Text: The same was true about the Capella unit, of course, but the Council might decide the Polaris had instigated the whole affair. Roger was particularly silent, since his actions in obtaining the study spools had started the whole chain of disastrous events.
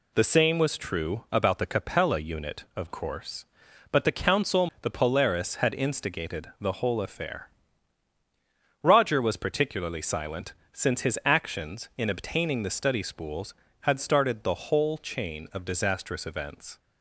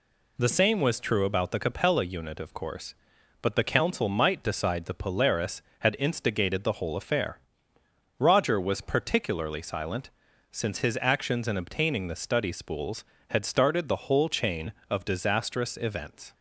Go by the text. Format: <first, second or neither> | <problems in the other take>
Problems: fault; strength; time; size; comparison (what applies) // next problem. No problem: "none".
second | skips "might decide"; at 4.7 s